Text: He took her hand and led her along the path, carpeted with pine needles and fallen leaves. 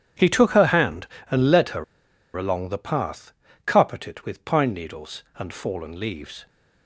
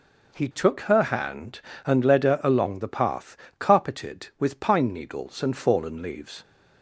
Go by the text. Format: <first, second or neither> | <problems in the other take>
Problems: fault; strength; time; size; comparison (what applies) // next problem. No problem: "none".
second | starts louder than the rest; strong; until 1.4 s; 9.5 dB // pauses between "her" and "along"; noticeable; at 1.8 s; 0.52 s long